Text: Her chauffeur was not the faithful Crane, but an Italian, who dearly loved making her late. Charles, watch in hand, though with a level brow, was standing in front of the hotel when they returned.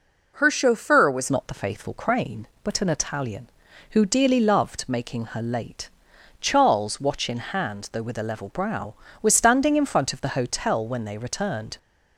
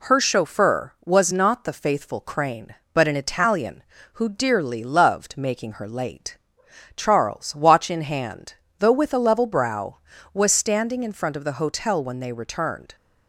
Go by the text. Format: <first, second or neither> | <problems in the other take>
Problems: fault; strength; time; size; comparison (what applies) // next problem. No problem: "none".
second | changes voice at "not"; from 1.2 s on; 10.5 s long